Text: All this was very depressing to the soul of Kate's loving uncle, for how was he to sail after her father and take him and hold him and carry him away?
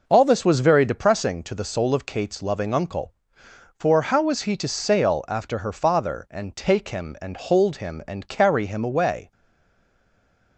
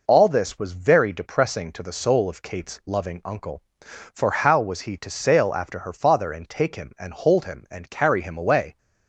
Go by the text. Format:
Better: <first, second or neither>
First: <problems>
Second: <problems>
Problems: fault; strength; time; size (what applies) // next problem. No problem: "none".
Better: second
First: stays silent after the last word; noticeable; from 9.3 s on; 1.2 s long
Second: none